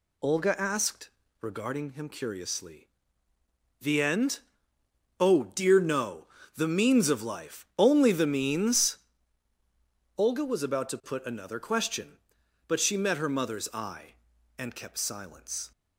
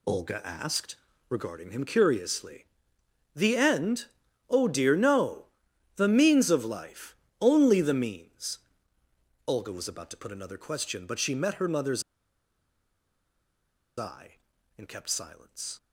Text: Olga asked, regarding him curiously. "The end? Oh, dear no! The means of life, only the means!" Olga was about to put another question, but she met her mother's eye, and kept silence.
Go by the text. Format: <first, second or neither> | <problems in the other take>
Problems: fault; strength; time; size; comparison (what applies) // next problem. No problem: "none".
first | pauses between "mother's" and "eye"; strong; at 12.0 s; 1.9 s long